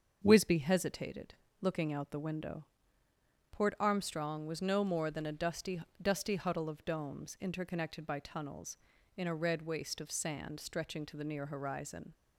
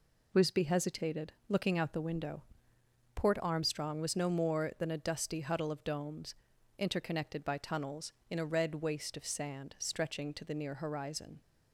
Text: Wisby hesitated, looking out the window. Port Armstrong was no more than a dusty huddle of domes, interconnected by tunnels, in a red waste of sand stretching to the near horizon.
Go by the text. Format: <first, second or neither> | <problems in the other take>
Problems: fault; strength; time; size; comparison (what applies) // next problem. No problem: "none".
second | starts louder than the rest; until 1.2 s; 7 dB // says "dusty" twice; at 5.9 s